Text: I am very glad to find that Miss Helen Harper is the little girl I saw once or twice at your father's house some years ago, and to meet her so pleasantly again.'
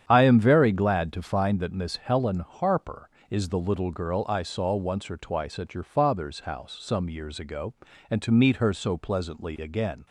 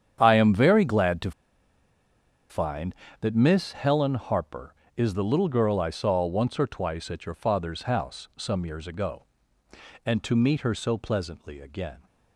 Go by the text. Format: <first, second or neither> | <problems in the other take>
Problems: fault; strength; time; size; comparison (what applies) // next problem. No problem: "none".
first | starts louder than the rest; strong; until 1.2 s; 8.5 dB; strong in the first // pauses between "to" and "find"; at 1.3 s; 1.1 s long